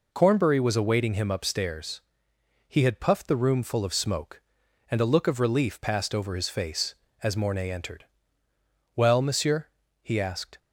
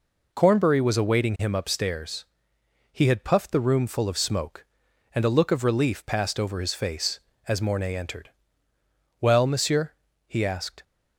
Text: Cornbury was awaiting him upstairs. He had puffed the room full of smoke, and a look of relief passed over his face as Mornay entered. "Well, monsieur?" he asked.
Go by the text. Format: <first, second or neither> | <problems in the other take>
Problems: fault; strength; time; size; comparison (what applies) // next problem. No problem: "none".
neither | none